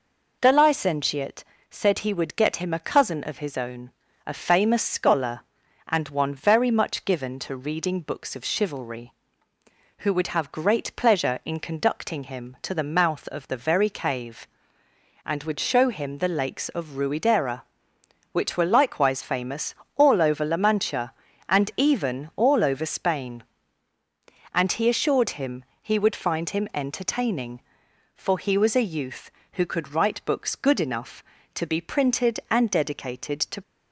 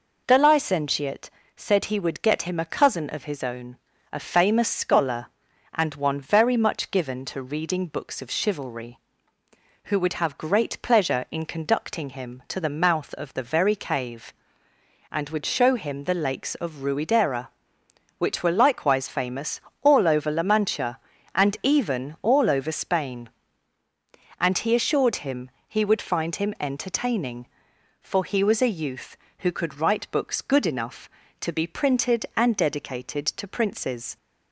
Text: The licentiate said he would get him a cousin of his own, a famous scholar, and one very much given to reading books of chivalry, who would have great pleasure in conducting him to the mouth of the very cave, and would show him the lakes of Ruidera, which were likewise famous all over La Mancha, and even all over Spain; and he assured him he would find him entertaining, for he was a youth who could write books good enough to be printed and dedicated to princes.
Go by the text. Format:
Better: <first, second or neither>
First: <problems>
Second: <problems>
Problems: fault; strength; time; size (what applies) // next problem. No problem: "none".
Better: second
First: pauses between "licentiate" and "said"; slight; at 1.4 s; 0.26 s long // pauses between "famous" and "all"; slight; at 19.7 s; 0.24 s long // pauses between "him" and "he"; slight; at 25.6 s; 0.16 s long // stops before "princes"; at 33.6 s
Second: pauses between "licentiate" and "said"; slight; at 1.3 s; 0.26 s long // pauses between "famous" and "all"; slight; at 19.5 s; 0.24 s long // pauses between "him" and "he"; slight; at 25.5 s; 0.16 s long